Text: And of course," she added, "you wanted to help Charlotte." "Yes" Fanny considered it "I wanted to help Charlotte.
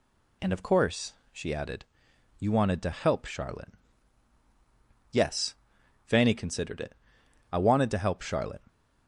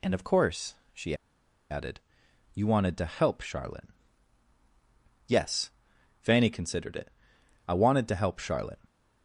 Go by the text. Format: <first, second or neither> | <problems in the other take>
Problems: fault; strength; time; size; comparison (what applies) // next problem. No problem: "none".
first | pauses between "she" and "added"; noticeable; at 1.1 s; 0.56 s long // pauses between "Yes" and "Fanny"; noticeable; at 5.7 s; 0.48 s long; noticeable in the first // pauses between "it" and "I"; noticeable; at 7.1 s; 0.56 s long; noticeable in the first